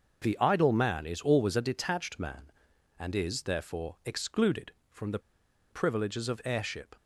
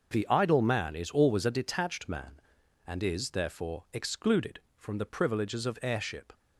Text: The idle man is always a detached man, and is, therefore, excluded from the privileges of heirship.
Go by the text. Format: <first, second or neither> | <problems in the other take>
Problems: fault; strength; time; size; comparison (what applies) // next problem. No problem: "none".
second | starts louder than the rest; noticeable; until 1.2 s; 6 dB; also in the second // pauses between "the" and "privileges"; noticeable; at 5.1 s; 0.51 s long